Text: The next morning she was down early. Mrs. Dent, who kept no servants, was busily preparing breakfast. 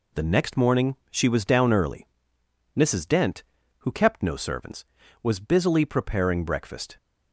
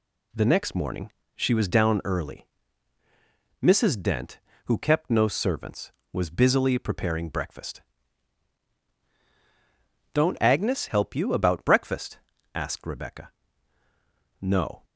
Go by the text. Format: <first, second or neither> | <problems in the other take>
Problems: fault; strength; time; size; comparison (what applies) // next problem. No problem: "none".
first | pauses between "morning" and "she"; slight; at 1.1 s; 0.24 s long; slight in the first // goes on to say "Don't Agnes help you about breakfast asked Rebecca No"; strong; from 10.1 s on; 4.7 s long